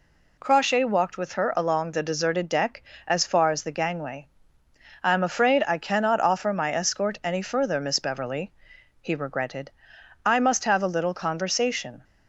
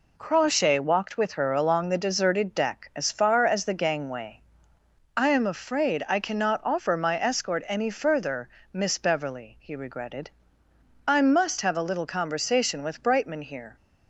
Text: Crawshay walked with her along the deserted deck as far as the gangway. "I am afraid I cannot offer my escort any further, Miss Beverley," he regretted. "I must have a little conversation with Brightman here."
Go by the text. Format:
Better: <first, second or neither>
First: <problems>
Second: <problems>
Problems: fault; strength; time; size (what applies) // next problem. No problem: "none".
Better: second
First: stops before "with Brightman here"; at 12.0 s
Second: none